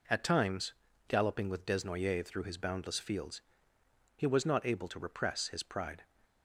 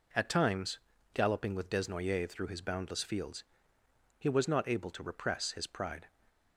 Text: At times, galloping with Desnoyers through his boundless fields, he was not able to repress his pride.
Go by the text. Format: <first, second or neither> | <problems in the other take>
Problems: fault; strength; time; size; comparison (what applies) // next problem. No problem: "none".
neither | none